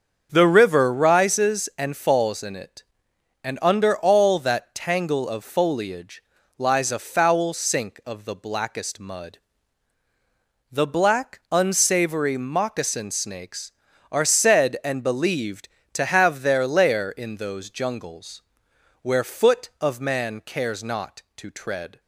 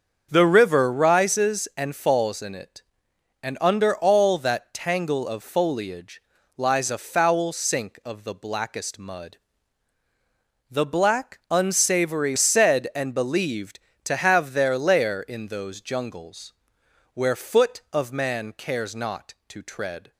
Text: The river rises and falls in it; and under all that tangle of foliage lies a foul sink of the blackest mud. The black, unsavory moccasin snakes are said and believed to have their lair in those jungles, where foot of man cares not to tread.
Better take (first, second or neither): first